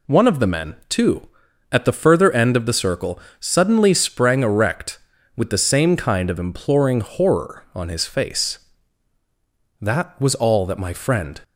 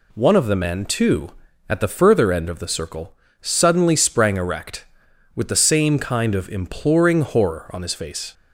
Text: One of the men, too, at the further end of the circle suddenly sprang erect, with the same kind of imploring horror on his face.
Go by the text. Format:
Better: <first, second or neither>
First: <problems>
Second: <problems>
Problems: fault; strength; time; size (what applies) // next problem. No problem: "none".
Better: second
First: pauses between "circle" and "suddenly"; slight; at 3.1 s; 0.20 s long // goes on to say "That was all that my friend"; from 9.8 s on; 1.6 s long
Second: pauses between "circle" and "suddenly"; slight; at 3.1 s; 0.26 s long